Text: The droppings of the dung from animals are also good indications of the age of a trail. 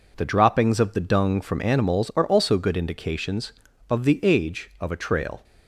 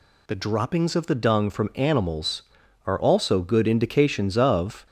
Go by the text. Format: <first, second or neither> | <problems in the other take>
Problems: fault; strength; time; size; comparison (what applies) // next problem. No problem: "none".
first | stops before "the age of a trail"; at 4.8 s